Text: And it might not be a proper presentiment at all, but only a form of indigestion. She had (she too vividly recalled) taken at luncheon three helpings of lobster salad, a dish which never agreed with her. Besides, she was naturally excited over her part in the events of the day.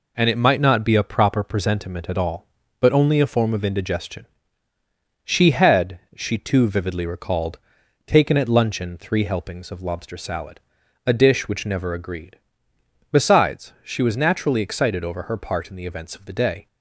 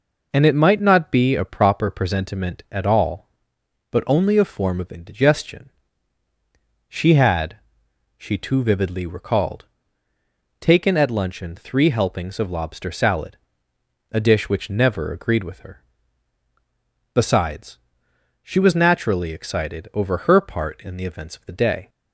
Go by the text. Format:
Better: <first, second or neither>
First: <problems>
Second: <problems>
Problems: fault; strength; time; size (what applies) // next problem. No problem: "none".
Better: second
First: skips "with her"; at 12.7 s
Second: none